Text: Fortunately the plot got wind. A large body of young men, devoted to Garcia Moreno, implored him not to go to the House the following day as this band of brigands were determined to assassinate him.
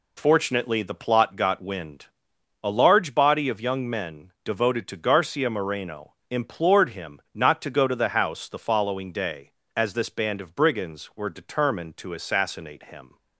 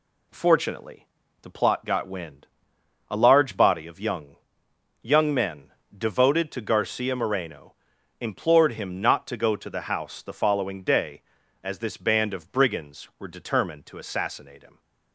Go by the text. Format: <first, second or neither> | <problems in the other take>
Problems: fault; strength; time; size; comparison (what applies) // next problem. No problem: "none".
first | pauses between "Fortunately" and "the"; slight; at 1.0 s; 0.36 s long // says "young" twice; at 5.0 s